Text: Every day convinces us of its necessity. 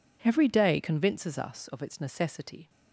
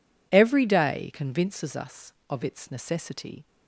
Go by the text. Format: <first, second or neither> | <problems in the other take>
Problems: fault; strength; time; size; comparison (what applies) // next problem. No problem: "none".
neither | none